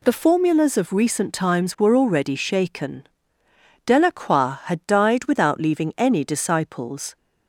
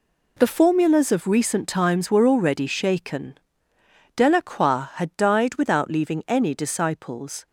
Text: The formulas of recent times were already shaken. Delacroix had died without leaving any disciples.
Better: first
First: none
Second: gets quieter; strong; throughout; 11 dB

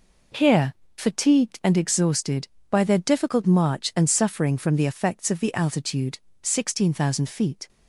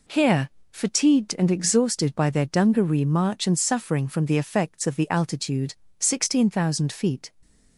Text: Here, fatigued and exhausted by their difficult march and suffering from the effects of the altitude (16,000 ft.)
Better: first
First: none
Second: says "dungaree" for "difficult"; at 2.4 s

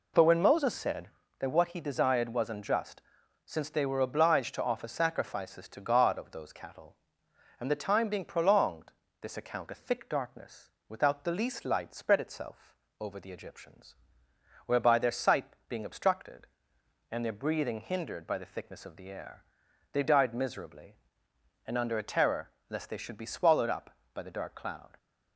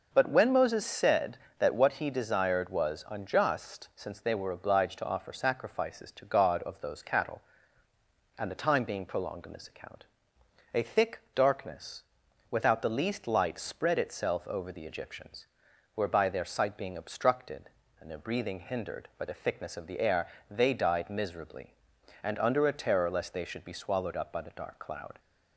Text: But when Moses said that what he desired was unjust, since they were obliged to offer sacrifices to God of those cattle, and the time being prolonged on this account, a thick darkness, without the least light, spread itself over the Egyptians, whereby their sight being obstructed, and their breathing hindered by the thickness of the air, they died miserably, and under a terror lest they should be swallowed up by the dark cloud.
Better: second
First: skips "on"; at 9.0 s // pauses between "itself" and "over"; slight; at 12.7 s; 0.26 s long // pauses between "sight" and "being"; slight; at 15.4 s; 0.22 s long // pauses between "terror" and "lest"; slight; at 22.4 s; 0.20 s long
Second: none

